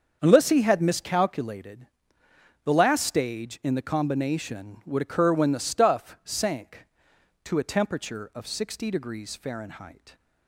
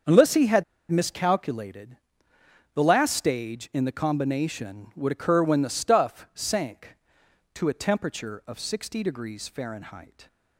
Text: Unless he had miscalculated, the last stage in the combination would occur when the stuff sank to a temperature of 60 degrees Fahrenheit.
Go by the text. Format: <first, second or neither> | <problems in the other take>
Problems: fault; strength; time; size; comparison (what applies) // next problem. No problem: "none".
first | starts louder than the rest; strong; until 1.3 s; 7 dB; also in the first // pauses between "had" and "miscalculated"; slight; at 0.6 s; 0.27 s long